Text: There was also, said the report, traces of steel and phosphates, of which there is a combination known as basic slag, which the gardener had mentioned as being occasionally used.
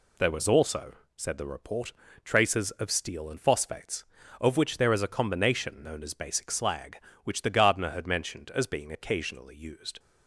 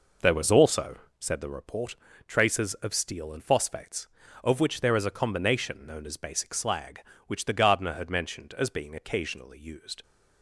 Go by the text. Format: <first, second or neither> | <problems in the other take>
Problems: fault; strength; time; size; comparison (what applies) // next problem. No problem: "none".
first | starts louder than the rest; noticeable; until 1.4 s; 5 dB